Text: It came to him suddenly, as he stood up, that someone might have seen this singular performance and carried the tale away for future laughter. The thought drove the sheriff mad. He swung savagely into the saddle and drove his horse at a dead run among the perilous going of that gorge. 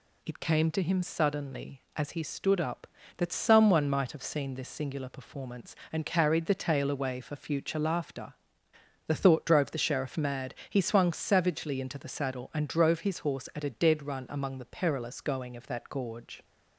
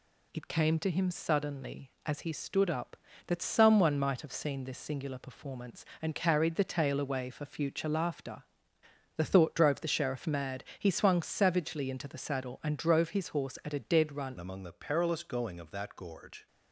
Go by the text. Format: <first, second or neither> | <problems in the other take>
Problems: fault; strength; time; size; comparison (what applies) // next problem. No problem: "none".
first | changes voice at "among"; from 14.3 s on; 2.1 s long